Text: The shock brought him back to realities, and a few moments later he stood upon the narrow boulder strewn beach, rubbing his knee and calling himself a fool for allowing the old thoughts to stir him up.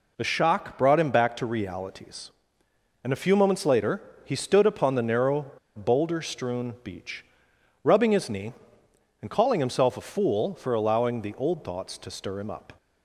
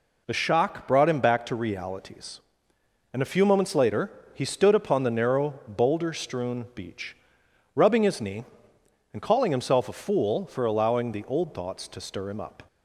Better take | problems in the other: second | pauses between "later" and "he"; slight; at 4.0 s; 0.22 s long; slight in the second // pauses between "narrow" and "boulder"; slight; at 5.5 s; 0.24 s long

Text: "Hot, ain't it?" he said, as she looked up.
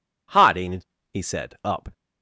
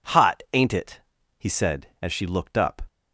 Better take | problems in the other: second | skips "as she looked"; at 1.5 s

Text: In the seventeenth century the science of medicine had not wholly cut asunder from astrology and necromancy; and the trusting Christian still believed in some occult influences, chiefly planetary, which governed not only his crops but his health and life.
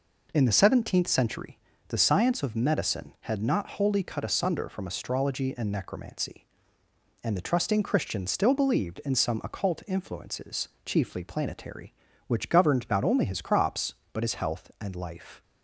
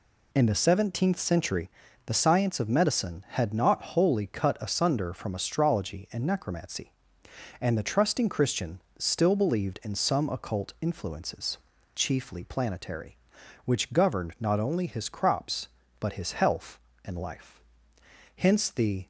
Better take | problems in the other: first | pauses between "century" and "the"; slight; at 1.6 s; 0.36 s long; slight in the first // pauses between "Christian" and "still"; slight; at 8.7 s; 0.18 s long // goes on to say "Hence the"; noticeable; from 18.3 s on; 0.72 s long

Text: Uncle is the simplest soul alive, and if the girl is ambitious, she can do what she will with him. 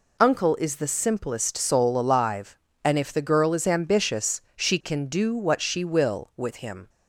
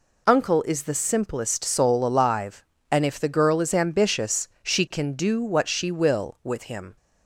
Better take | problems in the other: neither | none

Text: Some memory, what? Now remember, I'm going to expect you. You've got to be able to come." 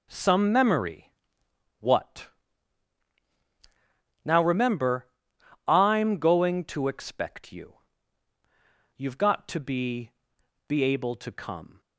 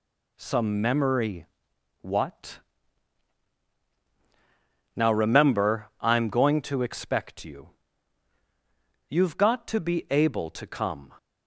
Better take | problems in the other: second | says "be" twice; at 10.6 s

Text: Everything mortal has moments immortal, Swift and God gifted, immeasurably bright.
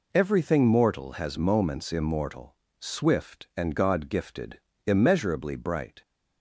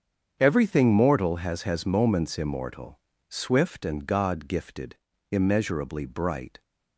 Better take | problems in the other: first | starts louder than the rest; strong; until 1.4 s; 7.5 dB // says "has" twice; at 1.6 s

